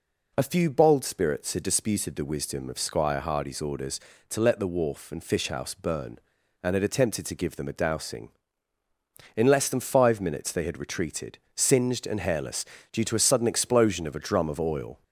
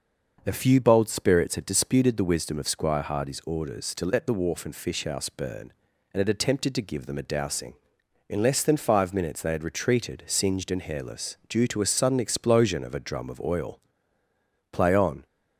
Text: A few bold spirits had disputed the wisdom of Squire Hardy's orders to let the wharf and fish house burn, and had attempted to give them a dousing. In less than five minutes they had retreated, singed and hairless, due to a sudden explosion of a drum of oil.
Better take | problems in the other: first | goes on to say "Play on"; from 14.7 s on; 0.54 s long

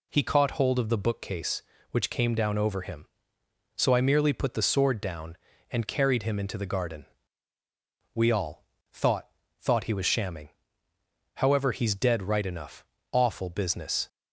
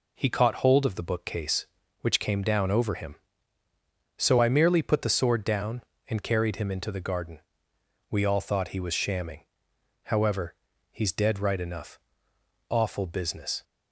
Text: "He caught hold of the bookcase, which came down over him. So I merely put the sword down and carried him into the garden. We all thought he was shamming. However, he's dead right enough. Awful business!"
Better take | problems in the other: second | pauses between "all" and "thought"; slight; at 8.6 s; 0.28 s long // says "thought" twice; at 9.5 s

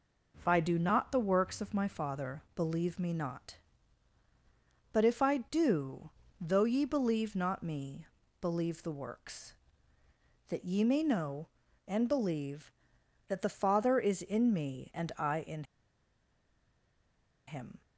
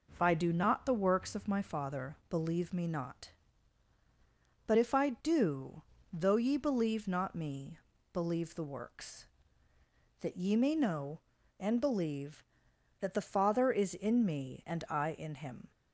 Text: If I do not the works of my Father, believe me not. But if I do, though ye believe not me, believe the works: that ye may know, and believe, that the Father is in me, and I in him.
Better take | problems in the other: second | pauses between "in" and "him"; strong; at 15.6 s; 1.8 s long

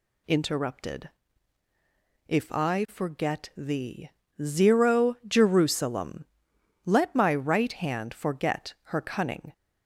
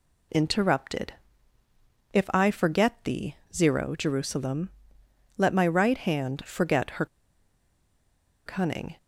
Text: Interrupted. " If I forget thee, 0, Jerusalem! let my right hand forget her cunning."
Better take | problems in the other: first | pauses between "her" and "cunning"; strong; at 7.0 s; 1.4 s long

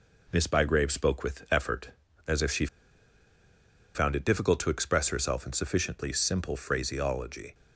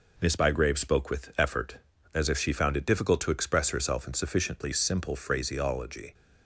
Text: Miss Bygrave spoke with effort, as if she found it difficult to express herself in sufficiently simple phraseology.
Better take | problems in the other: second | pauses between "she" and "found"; strong; at 2.6 s; 1.2 s long

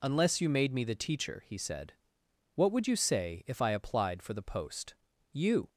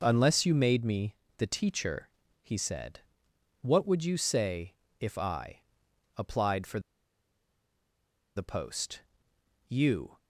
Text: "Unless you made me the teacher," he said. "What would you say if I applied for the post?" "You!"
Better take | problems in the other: first | pauses between "me" and "the"; slight; at 1.1 s; 0.24 s long // pauses between "say" and "if"; slight; at 4.7 s; 0.24 s long // pauses between "I" and "applied"; noticeable; at 5.5 s; 0.56 s long // pauses between "for" and "the"; strong; at 6.7 s; 1.5 s long

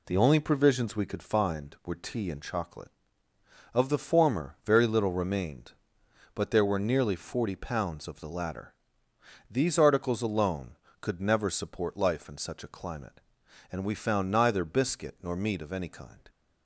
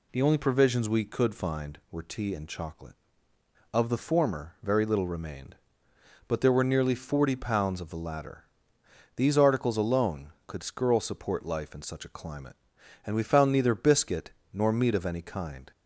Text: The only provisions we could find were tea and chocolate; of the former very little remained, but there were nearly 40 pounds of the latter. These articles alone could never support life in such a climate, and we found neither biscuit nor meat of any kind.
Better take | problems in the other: first | says "skirl" for "never"; at 10.6 s // pauses between "biscuit" and "nor"; slight; at 14.3 s; 0.20 s long

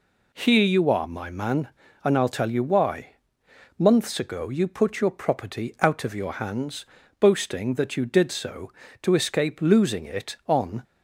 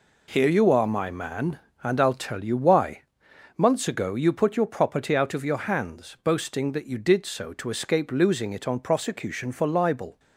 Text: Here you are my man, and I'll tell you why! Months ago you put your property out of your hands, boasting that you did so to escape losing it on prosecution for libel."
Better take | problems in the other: second | stops before "prosecution for libel"; at 10.8 s

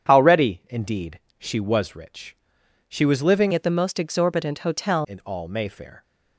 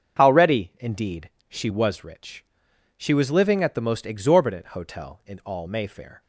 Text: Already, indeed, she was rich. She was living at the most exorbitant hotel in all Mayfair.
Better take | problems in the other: second | starts louder than the rest; strong; until 1.1 s; 9 dB; strong in the second // changes voice from "at" to "hotel"; from 3.5 to 5.0 s; 1.5 s long

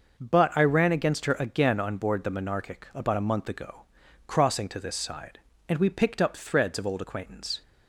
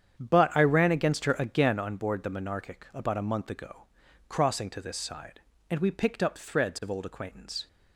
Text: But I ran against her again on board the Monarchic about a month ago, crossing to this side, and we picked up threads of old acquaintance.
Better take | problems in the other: first | starts louder than the rest; strong; until 1.8 s; 8.5 dB

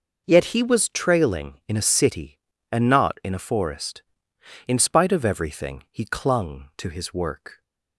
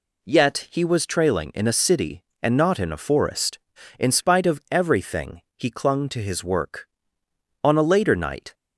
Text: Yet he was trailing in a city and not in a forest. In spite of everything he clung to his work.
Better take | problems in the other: first | goes on to say "On a later night"; noticeable; from 7.6 s on; 0.90 s long

